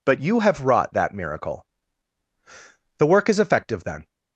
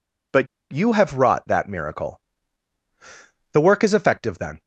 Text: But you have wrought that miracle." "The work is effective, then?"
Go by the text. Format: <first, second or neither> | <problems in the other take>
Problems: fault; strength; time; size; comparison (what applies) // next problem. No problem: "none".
first | pauses between "But" and "you"; slight; at 0.4 s; 0.24 s long